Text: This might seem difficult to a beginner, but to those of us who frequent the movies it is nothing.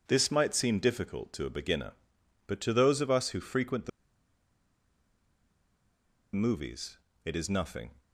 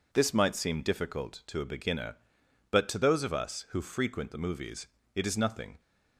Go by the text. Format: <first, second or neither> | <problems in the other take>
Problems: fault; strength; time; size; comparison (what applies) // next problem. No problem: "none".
second | pauses between "the" and "movies"; strong; at 3.8 s; 2.4 s long // pauses between "movies" and "it"; slight; at 6.9 s; 0.28 s long; slight in the second